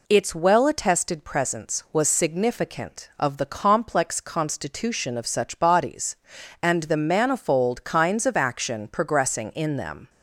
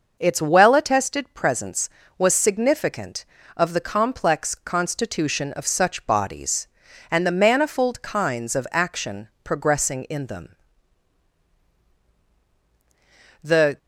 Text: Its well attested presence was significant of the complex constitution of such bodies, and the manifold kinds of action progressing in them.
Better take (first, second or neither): first